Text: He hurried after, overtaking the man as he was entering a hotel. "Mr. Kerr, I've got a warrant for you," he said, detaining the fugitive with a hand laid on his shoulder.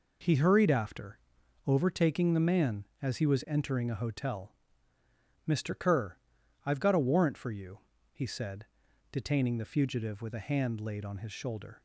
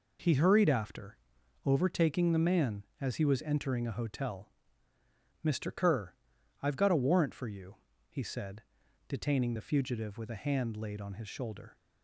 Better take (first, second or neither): neither